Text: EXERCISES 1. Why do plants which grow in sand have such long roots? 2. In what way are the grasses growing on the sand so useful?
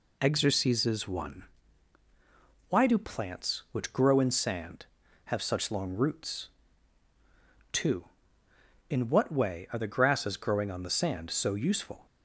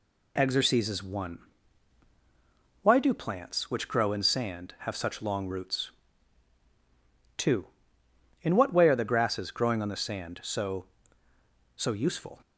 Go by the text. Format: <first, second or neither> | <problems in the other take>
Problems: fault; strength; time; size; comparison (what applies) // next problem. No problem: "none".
first | says "so" twice; at 11.7 s